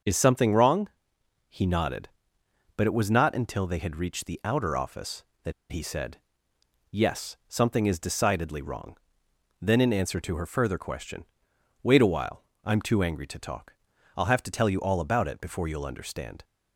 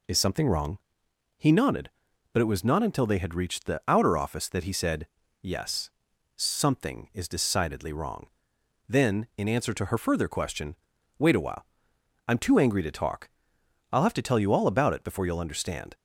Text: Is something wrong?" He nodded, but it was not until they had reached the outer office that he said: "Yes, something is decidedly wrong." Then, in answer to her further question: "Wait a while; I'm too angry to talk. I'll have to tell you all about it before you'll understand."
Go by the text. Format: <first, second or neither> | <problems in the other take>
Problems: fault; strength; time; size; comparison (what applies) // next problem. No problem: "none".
second | starts louder than the rest; until 1.6 s; 6.5 dB // pauses between "that" and "he"; slight; at 5.5 s; 0.18 s long